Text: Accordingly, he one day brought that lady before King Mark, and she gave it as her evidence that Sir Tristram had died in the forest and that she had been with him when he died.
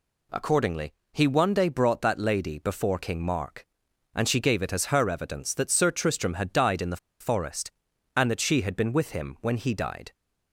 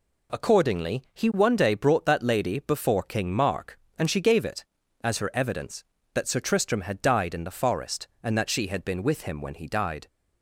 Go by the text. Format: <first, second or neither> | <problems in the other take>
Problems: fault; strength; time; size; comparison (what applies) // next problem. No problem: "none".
second | pauses between "the" and "forest"; slight; at 6.9 s; 0.24 s long